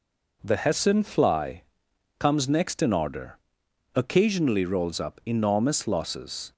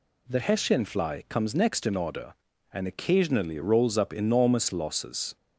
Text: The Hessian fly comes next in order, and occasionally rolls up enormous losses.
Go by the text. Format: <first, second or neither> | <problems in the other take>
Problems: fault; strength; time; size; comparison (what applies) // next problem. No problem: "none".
second | pauses between "fly" and "comes"; noticeable; at 1.6 s; 0.54 s long // skips "and"; at 3.6 s